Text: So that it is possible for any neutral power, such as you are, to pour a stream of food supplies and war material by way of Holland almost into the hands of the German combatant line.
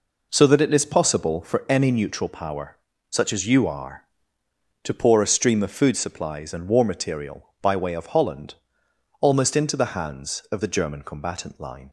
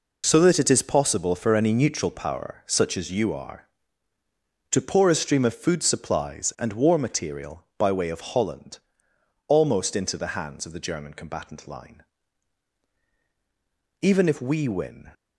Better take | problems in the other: first | pauses between "Holland" and "almost"; noticeable; at 8.7 s; 0.68 s long; noticeable in the first // goes on to say "Even if we win"; noticeable; from 14.0 s on; 1.1 s long

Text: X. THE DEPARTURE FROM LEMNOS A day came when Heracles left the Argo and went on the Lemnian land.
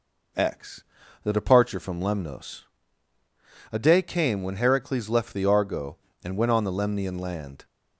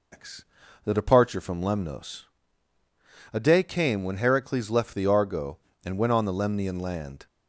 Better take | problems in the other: first | loses the start of "X"; at 0.1 s; 160 ms // pauses between "LEMNOS" and "A"; at 2.2 s; 1.0 s long; also in the first

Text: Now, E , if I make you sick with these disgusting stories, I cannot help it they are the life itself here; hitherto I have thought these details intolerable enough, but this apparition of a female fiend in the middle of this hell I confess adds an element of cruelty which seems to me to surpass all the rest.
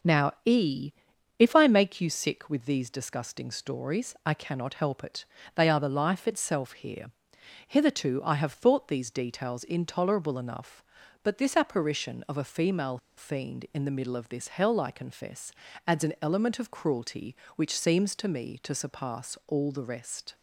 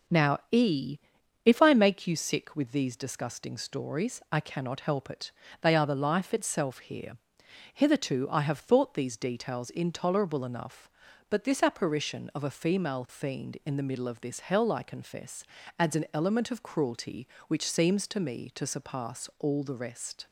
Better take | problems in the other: second | pauses between "it" and "they"; slight; at 5.2 s; 0.30 s long; slight in the second // pauses between "female" and "fiend"; slight; at 12.9 s; 0.20 s long // pauses between "confess" and "adds"; slight; at 15.5 s; 0.34 s long; slight in the second

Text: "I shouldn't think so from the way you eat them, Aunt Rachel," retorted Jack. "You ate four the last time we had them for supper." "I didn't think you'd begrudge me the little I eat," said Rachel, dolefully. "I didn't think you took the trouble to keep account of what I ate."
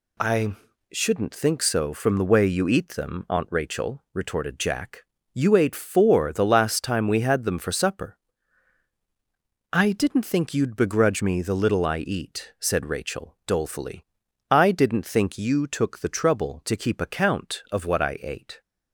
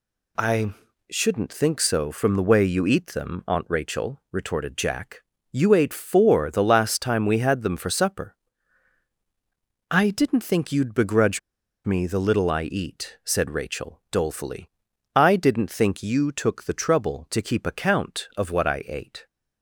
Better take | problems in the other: first | pauses between "I" and "shouldn't"; slight; at 0.7 s; 0.36 s long; slight in the first // pauses between "begrudge" and "me"; noticeable; at 11.3 s; 0.46 s long

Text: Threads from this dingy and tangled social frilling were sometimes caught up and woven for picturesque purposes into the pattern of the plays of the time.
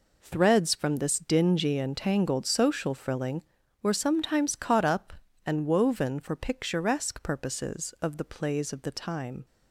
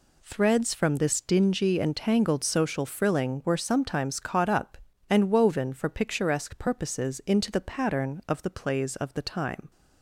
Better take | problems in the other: second | skips "into the pattern"; at 7.9 s

